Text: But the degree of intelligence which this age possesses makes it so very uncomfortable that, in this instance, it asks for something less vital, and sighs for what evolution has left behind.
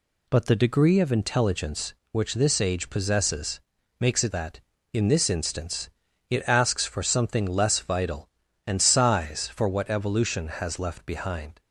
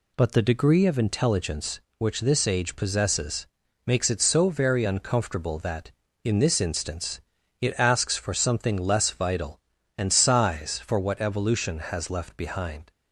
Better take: second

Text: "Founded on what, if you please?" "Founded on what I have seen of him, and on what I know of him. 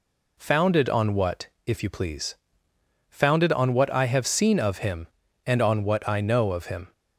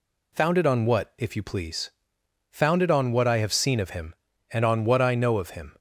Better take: neither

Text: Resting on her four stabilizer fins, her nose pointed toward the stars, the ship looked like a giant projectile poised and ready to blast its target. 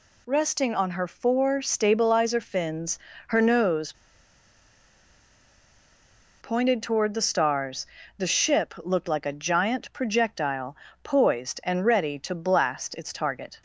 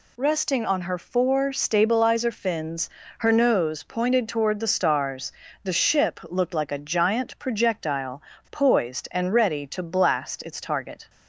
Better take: second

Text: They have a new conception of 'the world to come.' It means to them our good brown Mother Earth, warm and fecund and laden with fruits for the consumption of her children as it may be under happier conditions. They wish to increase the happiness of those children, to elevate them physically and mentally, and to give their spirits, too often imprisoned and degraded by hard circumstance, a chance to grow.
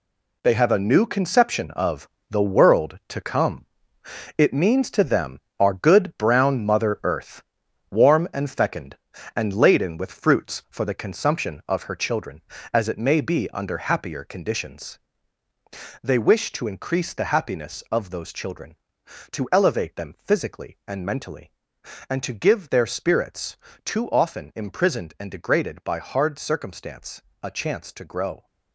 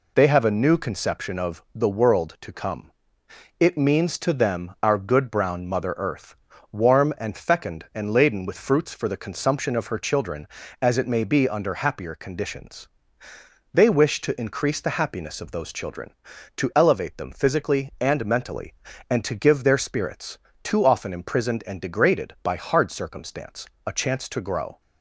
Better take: second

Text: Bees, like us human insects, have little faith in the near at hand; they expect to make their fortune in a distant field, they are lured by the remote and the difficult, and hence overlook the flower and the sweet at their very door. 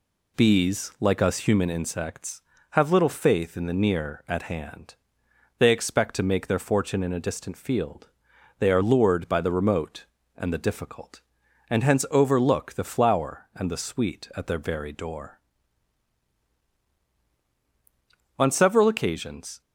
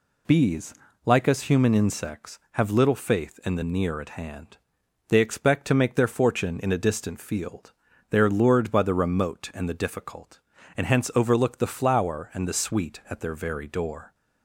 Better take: second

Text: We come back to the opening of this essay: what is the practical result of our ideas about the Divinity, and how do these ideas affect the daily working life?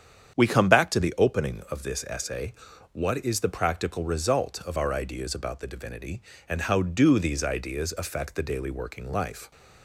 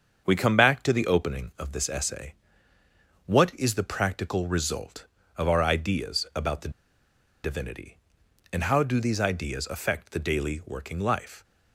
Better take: first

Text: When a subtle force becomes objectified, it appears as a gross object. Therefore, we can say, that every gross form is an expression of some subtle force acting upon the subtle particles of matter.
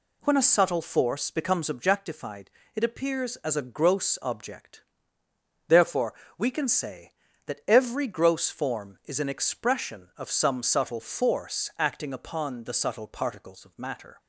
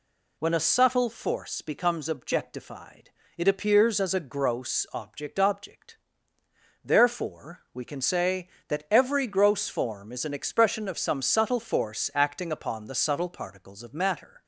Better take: first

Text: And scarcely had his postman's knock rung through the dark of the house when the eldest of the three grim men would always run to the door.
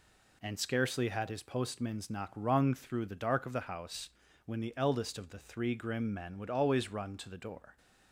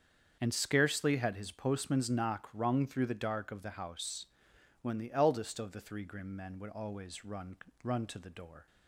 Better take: first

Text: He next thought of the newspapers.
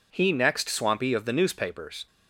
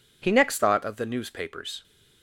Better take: second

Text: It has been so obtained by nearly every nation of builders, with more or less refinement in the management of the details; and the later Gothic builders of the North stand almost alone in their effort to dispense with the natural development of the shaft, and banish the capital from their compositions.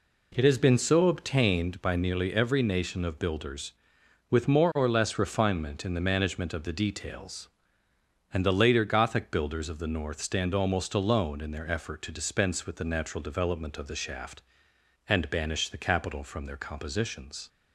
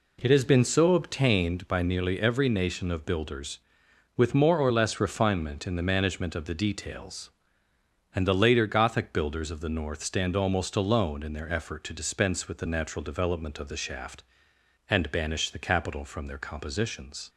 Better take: neither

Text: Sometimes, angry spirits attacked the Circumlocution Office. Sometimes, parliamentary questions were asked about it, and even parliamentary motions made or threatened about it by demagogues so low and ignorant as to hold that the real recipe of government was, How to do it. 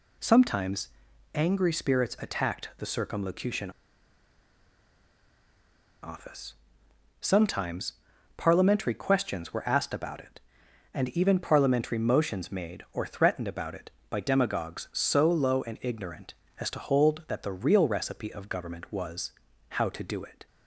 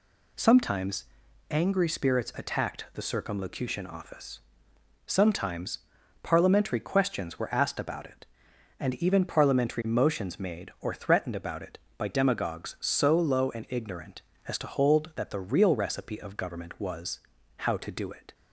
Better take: second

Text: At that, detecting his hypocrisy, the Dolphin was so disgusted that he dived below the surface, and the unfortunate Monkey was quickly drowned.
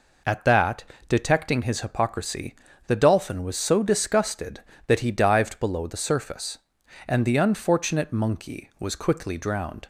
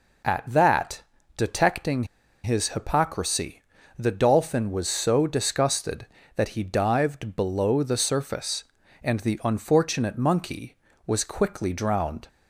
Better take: first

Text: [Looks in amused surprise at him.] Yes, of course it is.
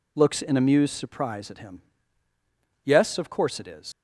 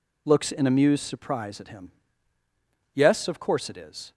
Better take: second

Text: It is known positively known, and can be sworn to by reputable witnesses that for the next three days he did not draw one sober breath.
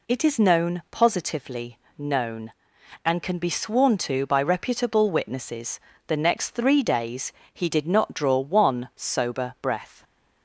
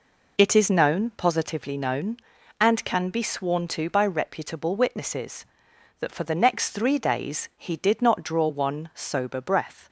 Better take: second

